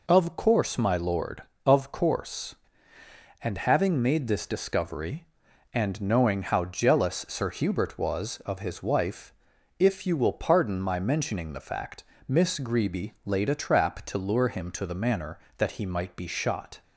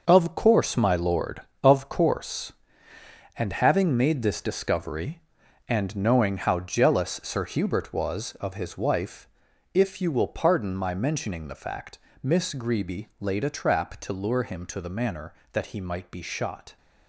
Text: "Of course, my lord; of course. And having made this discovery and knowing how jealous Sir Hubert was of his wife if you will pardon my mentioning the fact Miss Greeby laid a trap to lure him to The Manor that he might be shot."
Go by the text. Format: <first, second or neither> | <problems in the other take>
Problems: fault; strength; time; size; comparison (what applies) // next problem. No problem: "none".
first | gets quieter; strong; throughout; 9.5 dB // pauses between "wife" and "if"; noticeable; at 9.2 s; 0.46 s long; noticeable in the first // pauses between "fact" and "Miss"; slight; at 11.9 s; 0.24 s long; slight in the first